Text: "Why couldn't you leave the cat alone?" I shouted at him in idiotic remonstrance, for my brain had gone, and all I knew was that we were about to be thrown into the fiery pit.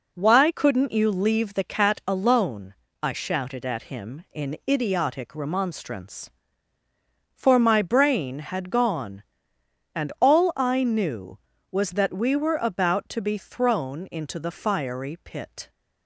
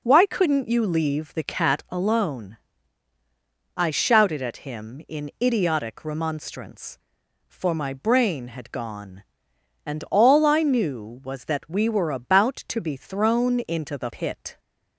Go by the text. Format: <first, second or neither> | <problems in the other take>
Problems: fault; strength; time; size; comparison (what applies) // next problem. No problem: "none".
first | skips "fiery"; at 14.1 s